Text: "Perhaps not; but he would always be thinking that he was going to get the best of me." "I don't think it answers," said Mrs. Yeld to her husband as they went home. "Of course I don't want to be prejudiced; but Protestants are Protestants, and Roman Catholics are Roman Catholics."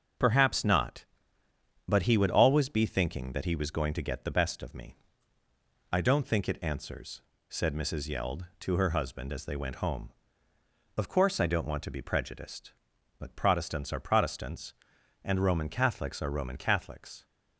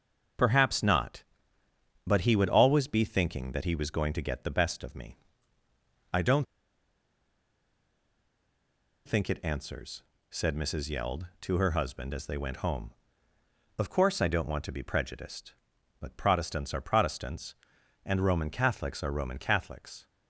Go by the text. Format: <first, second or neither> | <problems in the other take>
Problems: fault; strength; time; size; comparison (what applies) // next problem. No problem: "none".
first | starts louder than the rest; until 2.2 s; 6.5 dB; also in the first // pauses between "don't" and "think"; strong; at 6.4 s; 2.6 s long